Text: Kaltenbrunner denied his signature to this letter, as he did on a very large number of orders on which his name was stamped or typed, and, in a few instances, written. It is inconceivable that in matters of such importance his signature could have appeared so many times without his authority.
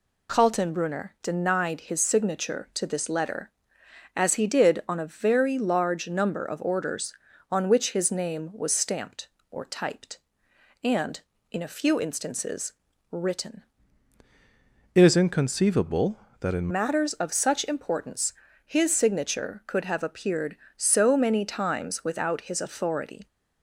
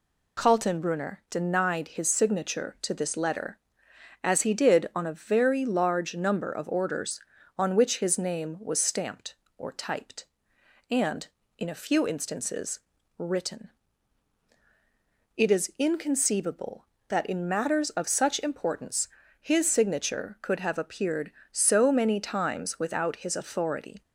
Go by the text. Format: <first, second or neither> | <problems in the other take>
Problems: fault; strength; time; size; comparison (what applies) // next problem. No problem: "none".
second | changes voice from "It" to "in"; from 14.9 to 16.6 s; 1.7 s long // pauses between "importance" and "his"; slight; at 18.3 s; 0.32 s long; slight in the second